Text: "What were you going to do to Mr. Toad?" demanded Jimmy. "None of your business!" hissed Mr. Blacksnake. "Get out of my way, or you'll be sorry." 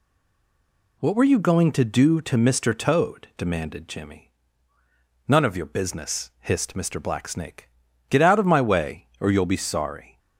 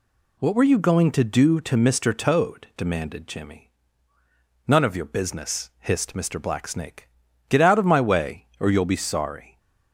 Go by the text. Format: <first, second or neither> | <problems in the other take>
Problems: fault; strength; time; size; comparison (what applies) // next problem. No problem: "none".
second | stays silent before the first word; until 0.9 s; 0.9 s long